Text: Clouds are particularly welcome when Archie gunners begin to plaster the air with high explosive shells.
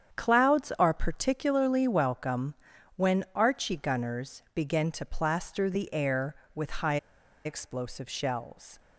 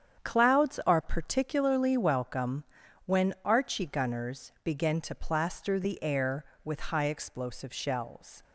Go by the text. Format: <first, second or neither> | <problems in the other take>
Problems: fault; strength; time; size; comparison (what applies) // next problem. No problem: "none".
second | starts louder than the rest; strong; until 1.2 s; 8.5 dB; strong in the second // pauses between "welcome" and "when"; at 2.5 s; 0.44 s long; also in the second // pauses between "high" and "explosive"; noticeable; at 6.9 s; 0.47 s long